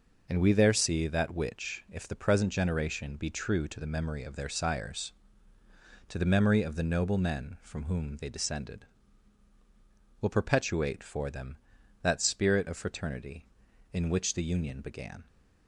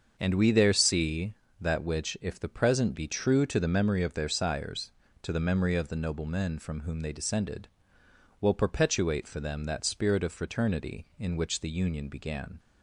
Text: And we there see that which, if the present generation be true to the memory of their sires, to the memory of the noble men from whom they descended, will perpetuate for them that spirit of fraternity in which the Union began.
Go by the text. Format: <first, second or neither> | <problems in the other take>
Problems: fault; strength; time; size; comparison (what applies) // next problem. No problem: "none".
first | starts louder than the rest; until 1.1 s; 6.5 dB // skips "generation"; at 2.9 s